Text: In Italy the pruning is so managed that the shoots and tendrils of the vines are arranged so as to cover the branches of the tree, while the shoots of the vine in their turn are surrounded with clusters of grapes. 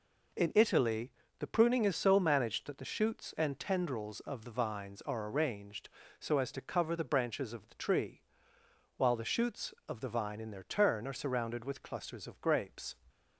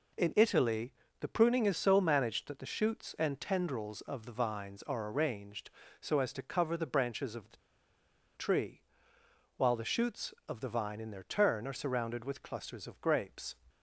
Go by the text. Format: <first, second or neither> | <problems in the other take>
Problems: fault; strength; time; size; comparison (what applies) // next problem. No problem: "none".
first | pauses between "Italy" and "the"; slight; at 0.9 s; 0.30 s long; slight in the first // pauses between "the" and "tree"; noticeable; at 7.5 s; 0.79 s long